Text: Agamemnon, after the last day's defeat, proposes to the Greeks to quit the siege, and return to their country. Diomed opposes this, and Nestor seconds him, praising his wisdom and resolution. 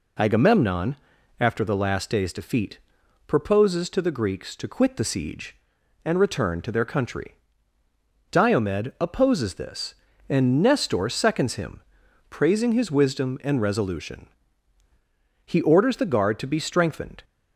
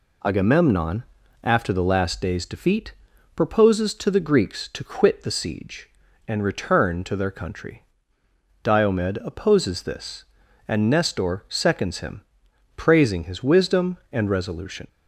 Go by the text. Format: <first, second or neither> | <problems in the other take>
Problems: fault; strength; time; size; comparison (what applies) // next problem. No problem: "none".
second | goes on to say "He orders the guard to be strengthened"; strong; from 15.4 s on; 1.7 s long